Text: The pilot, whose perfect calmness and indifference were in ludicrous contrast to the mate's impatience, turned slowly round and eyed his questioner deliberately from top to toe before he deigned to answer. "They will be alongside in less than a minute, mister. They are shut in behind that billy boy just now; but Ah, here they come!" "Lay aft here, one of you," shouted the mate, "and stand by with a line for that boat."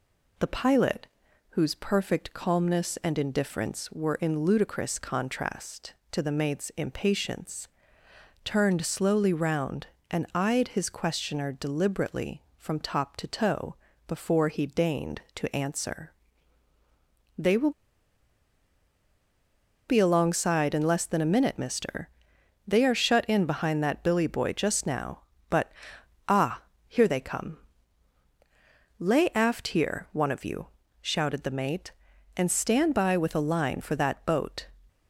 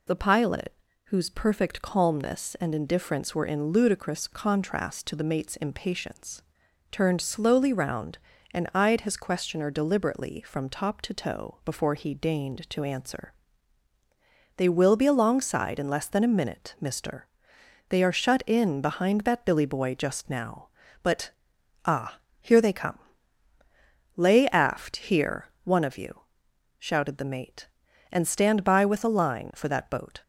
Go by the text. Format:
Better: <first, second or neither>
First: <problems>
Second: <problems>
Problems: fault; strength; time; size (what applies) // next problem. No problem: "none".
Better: second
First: pauses between "toe" and "before"; slight; at 13.7 s; 0.30 s long // pauses between "will" and "be"; strong; at 17.7 s; 2.1 s long // pauses between "but" and "Ah"; noticeable; at 25.7 s; 0.56 s long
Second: pauses between "but" and "Ah"; noticeable; at 21.3 s; 0.52 s long